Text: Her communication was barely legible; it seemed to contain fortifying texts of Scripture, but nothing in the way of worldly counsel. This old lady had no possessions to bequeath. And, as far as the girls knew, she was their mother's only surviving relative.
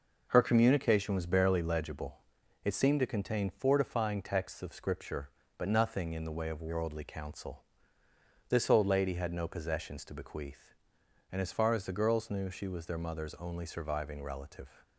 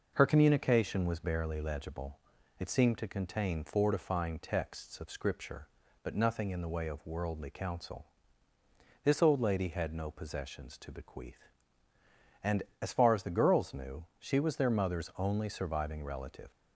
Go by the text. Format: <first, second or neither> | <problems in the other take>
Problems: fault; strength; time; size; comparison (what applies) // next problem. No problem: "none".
neither | none